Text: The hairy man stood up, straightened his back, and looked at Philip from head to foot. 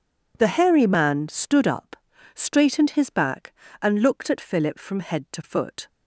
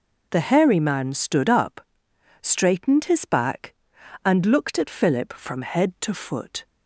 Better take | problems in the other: neither | none

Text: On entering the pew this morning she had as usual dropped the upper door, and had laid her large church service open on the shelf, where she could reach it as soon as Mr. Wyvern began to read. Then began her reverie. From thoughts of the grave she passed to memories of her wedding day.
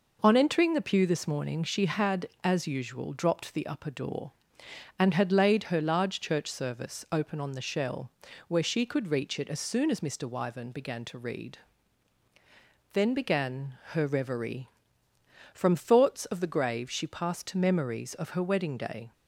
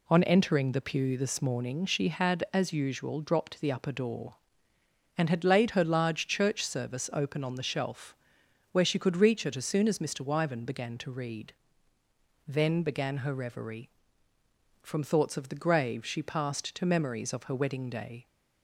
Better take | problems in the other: second | says "shell" for "shelf"; at 7.6 s // pauses between "began" and "her"; slight; at 13.7 s; 0.18 s long

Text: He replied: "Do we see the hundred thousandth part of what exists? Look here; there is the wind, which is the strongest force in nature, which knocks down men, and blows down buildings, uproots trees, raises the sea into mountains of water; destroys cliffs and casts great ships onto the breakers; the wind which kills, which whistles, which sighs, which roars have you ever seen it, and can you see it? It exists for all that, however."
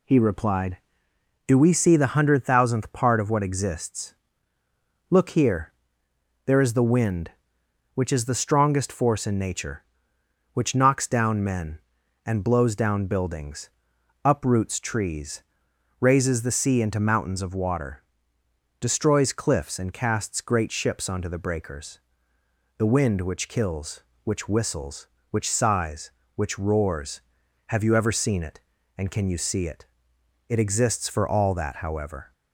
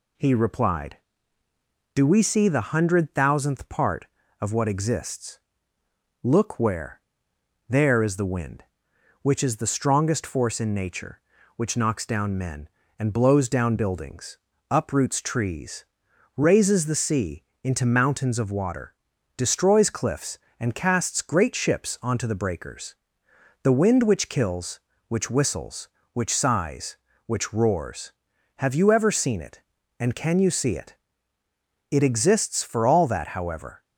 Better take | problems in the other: first | says "where" for "here"; at 6.5 s // pauses between "sea" and "into"; slight; at 17.4 s; 0.20 s long

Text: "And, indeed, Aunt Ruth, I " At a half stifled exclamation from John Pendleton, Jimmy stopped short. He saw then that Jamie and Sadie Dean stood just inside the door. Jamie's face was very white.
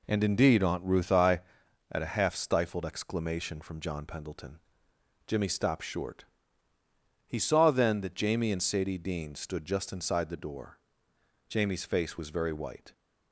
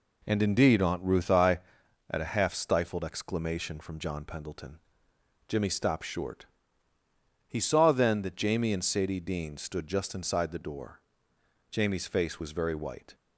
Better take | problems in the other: neither | none

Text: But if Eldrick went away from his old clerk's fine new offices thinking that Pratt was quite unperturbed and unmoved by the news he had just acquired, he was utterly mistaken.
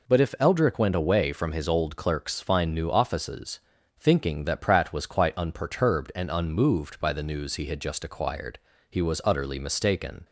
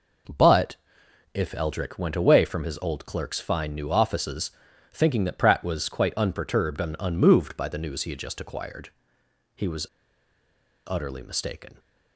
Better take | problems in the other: first | pauses between "But" and "if"; noticeable; at 0.7 s; 0.58 s long // pauses between "offices" and "thinking"; at 4.5 s; 0.42 s long; also in the first // pauses between "was" and "utterly"; at 9.8 s; 1.0 s long

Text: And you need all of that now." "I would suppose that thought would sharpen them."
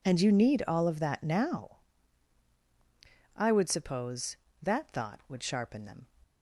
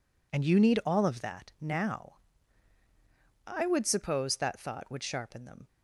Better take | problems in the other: neither | none

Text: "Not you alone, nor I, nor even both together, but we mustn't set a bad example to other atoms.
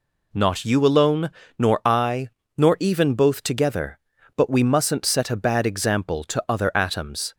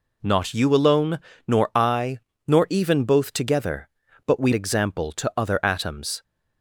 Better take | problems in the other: first | skips "mustn't set a bad"; at 4.5 s

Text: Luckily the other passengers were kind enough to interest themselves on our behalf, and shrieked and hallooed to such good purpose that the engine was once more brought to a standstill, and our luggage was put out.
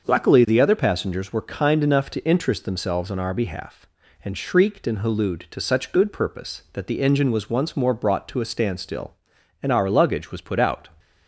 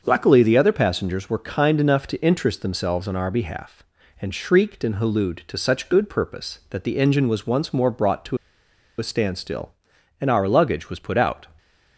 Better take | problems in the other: first | starts louder than the rest; until 1.0 s; 6.5 dB; also in the first // pauses between "to" and "a"; noticeable; at 8.3 s; 0.61 s long

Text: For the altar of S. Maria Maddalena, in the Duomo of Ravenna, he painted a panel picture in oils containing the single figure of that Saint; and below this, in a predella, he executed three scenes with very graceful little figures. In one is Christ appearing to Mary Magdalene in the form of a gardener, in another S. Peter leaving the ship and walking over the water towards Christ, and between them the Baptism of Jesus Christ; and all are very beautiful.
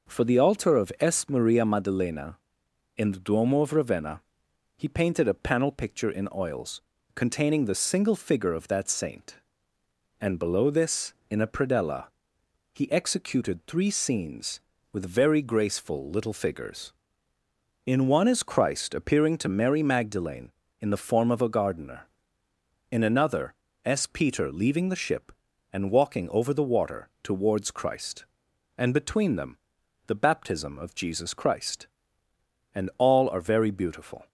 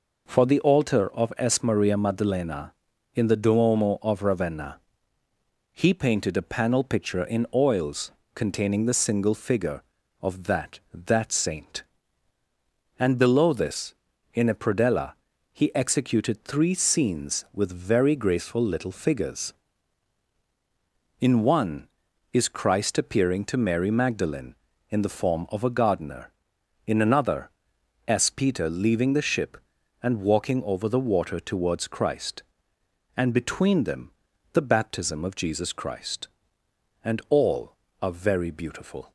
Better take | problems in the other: first | pauses between "oils" and "containing"; slight; at 8.1 s; 0.24 s long; slight in the first // says "that" twice; at 10.9 s // pauses between "another" and "S"; noticeable; at 27.4 s; 0.60 s long; slight in the first // pauses between "them" and "the"; at 34.1 s; 0.42 s long; noticeable in the first

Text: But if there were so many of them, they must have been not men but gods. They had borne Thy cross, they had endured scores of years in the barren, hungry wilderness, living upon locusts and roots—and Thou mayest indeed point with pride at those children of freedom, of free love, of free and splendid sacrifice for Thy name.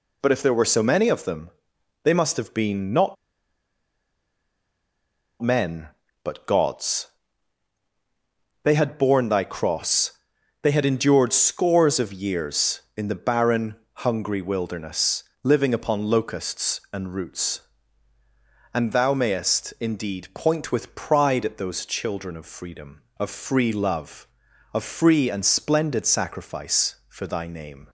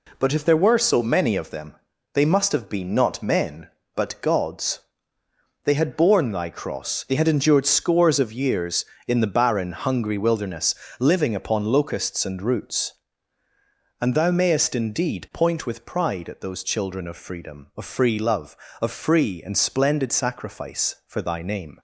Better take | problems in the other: second | pauses between "not" and "men"; strong; at 3.1 s; 2.2 s long

